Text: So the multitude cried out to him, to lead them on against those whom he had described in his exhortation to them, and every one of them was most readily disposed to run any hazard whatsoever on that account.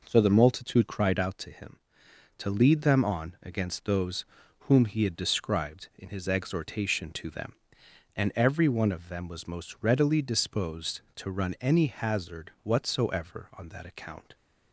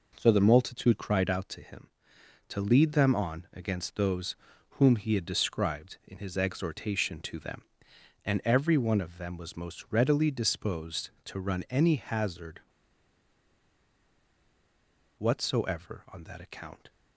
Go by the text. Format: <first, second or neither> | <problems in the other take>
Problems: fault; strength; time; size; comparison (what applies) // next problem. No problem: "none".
first | pauses between "those" and "whom"; slight; at 4.3 s; 0.36 s long; slight in the first // pauses between "hazard" and "whatsoever"; strong; at 12.5 s; 2.5 s long